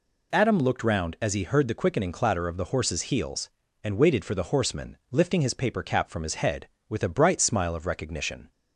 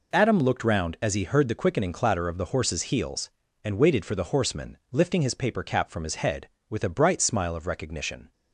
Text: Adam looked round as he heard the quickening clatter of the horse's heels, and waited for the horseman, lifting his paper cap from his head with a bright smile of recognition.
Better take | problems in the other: first | gets quieter; strong; throughout; 10.5 dB

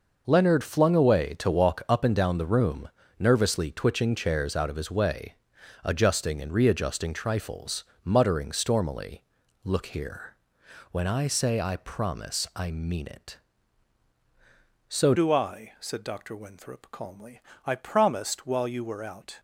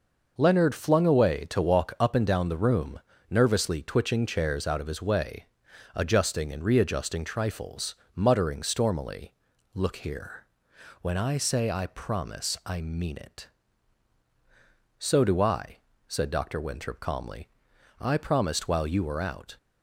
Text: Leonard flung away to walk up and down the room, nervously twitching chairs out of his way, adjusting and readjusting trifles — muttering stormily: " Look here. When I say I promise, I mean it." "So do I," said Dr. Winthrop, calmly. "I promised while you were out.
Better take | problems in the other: second | changes voice at "do"; from 15.1 s on; 4.2 s long

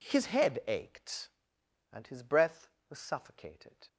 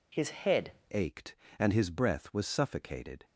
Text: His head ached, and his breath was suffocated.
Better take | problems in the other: first | changes voice at "ached"; from 0.9 s on; 2.3 s long

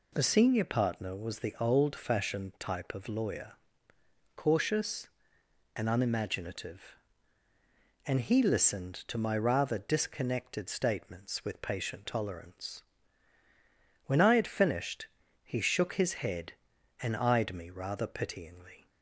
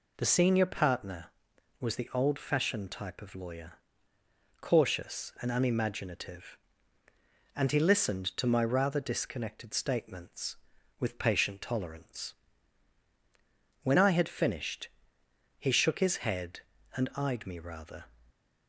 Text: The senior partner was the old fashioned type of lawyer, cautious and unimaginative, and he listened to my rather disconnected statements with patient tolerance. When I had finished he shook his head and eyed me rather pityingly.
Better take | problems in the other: first | pauses between "finished" and "he"; noticeable; at 14.8 s; 0.68 s long; slight in the first // stops before "pityingly"; at 18.3 s

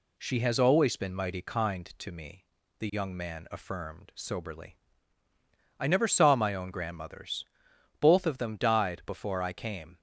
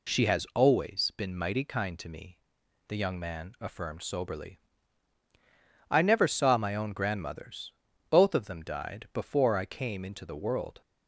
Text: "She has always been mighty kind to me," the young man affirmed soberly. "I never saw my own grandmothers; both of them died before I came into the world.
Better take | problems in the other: second | stops before "into the world"; at 9.9 s

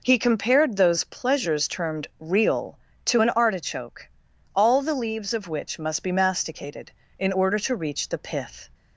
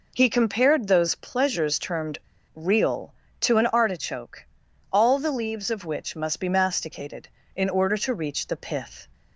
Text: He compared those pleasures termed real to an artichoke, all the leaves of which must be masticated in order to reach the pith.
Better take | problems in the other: first | pauses between "termed" and "real"; slight; at 2.1 s; 0.34 s long

